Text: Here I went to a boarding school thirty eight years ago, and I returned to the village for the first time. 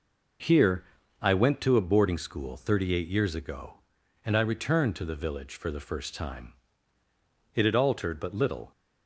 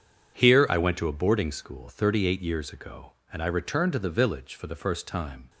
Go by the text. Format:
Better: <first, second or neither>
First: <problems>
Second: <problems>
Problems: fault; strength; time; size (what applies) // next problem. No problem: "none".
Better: second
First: pauses between "Here" and "I"; at 0.8 s; 0.38 s long // goes on to say "It had altered but little"; noticeable; from 7.5 s on; 1.1 s long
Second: none